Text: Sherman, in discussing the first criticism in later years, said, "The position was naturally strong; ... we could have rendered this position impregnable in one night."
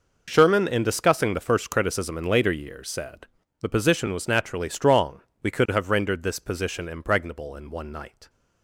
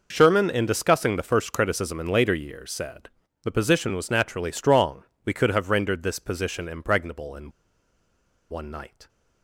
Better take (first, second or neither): first